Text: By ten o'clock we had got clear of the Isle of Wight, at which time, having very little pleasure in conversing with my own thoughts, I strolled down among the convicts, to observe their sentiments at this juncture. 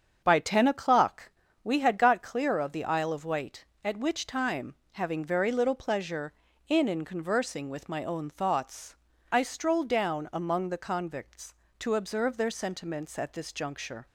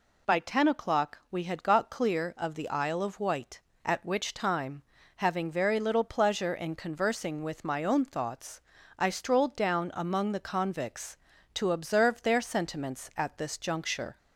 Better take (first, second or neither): second